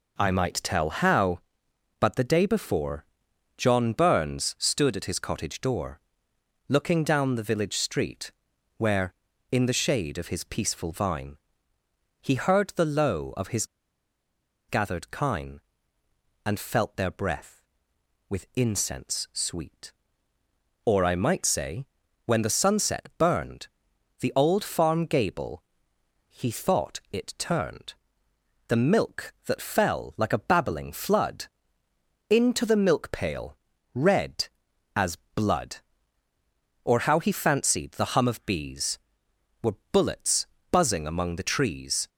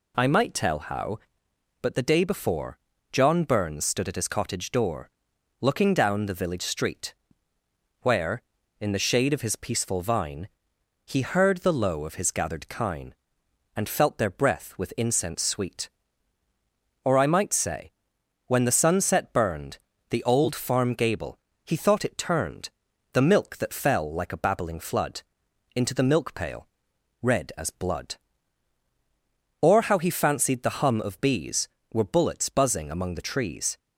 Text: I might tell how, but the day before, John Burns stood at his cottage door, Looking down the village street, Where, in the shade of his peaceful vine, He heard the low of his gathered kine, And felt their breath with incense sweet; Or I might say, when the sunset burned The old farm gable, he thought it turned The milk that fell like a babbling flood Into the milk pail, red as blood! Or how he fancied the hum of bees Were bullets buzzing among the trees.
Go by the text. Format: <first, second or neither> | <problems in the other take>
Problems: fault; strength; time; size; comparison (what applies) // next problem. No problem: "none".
second | pauses between "his" and "gathered"; at 13.6 s; 1.0 s long // pauses between "burned" and "The"; noticeable; at 23.6 s; 0.52 s long; slight in the second // pauses between "turned" and "The"; noticeable; at 27.9 s; 0.72 s long; also in the second // pauses between "flood" and "Into"; noticeable; at 31.4 s; 0.84 s long; noticeable in the second // pauses between "as" and "blood"; slight; at 35.1 s; 0.18 s long // pauses between "Were" and "bullets"; slight; at 39.7 s; 0.16 s long // pauses between "bullets" and "buzzing"; slight; at 40.4 s; 0.24 s long